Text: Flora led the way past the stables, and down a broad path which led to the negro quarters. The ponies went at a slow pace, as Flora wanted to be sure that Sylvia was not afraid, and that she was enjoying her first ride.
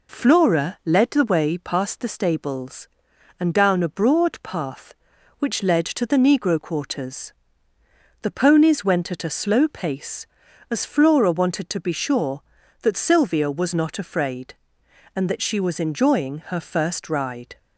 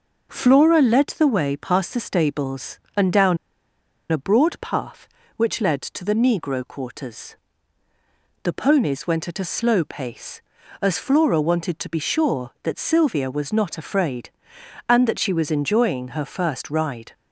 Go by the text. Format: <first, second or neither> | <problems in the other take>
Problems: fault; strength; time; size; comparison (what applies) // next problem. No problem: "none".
first | pauses between "down" and "a"; noticeable; at 3.3 s; 0.73 s long